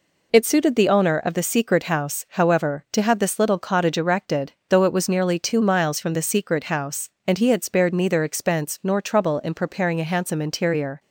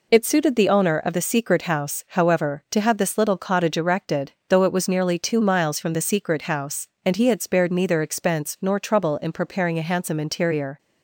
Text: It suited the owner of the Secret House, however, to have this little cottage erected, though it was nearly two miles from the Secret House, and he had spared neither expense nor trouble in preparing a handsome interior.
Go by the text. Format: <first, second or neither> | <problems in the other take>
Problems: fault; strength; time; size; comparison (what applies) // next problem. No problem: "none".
neither | none